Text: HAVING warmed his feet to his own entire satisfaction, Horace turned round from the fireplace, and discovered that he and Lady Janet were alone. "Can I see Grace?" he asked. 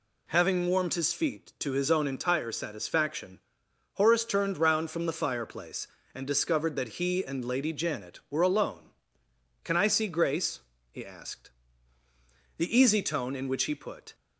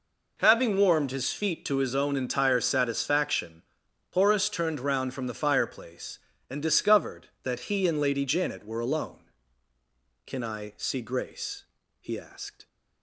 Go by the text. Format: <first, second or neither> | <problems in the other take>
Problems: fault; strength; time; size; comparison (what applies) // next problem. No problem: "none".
second | goes on to say "The easy tone in which he put"; from 12.5 s on; 1.5 s long